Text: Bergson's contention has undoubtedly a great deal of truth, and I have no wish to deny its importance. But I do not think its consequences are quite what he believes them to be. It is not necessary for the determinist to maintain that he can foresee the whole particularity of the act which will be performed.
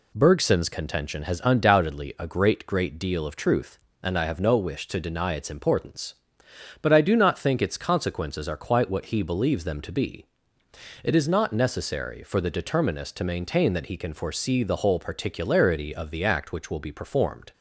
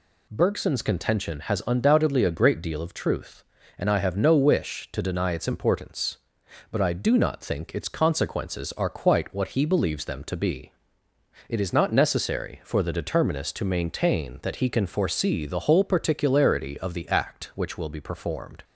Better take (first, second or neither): second